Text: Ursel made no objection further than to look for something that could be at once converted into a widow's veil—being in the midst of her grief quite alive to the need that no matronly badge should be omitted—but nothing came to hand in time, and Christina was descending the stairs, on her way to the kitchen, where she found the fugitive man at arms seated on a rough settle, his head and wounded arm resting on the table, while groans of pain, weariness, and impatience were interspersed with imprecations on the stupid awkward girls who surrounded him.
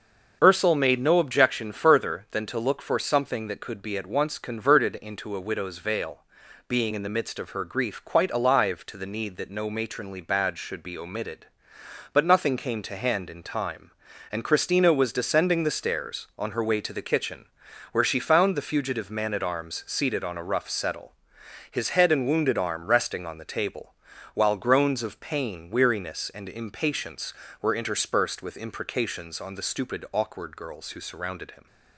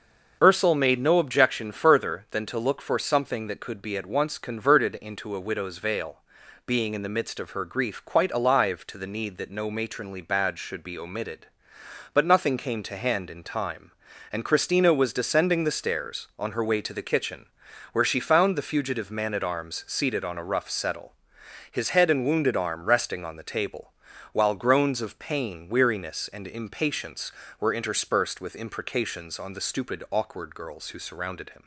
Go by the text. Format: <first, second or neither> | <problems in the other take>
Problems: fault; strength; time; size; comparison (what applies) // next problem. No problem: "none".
neither | starts louder than the rest; the same in both